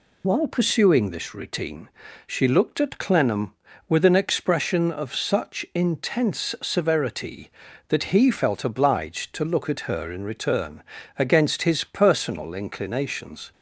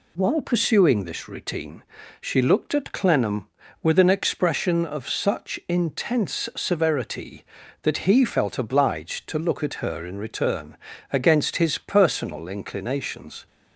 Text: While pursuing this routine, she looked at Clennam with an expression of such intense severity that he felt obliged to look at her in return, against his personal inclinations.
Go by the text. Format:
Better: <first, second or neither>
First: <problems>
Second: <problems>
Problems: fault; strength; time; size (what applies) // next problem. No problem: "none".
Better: second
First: loses the start of "While"; at 0.2 s; 35 ms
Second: none